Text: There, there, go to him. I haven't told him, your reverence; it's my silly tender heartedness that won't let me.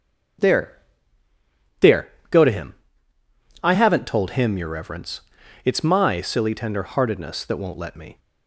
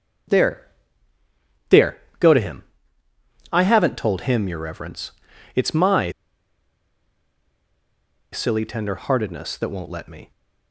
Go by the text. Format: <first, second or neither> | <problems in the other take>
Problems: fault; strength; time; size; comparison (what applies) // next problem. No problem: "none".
first | starts louder than the rest; strong; until 2.5 s; 7 dB; strong in the first // pauses between "my" and "silly"; strong; at 6.1 s; 2.2 s long